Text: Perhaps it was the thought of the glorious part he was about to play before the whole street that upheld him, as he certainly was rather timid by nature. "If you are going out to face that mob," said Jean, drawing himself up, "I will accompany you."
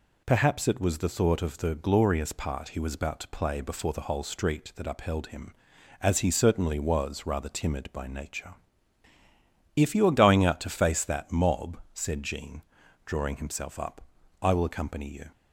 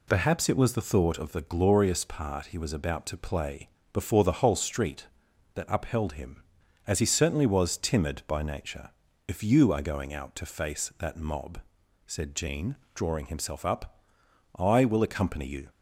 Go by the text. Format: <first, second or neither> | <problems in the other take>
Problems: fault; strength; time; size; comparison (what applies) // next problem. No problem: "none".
first | pauses between "play" and "before"; slight; at 3.6 s; 0.24 s long // skips "rather"; at 7.7 s